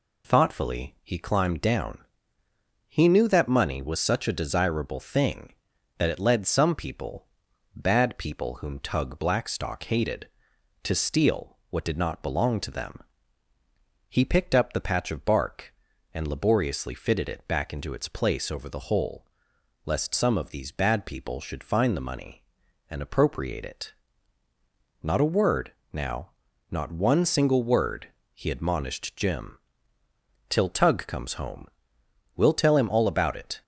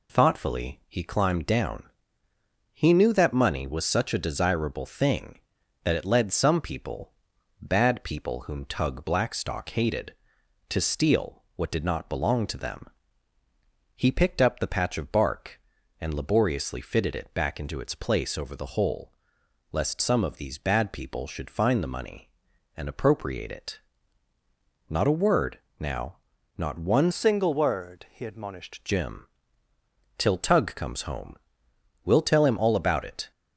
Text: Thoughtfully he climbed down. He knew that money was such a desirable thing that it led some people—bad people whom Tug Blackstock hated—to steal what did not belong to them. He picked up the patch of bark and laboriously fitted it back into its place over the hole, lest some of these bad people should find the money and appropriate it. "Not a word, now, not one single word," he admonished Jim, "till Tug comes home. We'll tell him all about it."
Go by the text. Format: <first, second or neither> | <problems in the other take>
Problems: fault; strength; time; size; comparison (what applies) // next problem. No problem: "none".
first | changes voice from "single" to "admonished"; from 27.1 to 28.8 s; 1.7 s long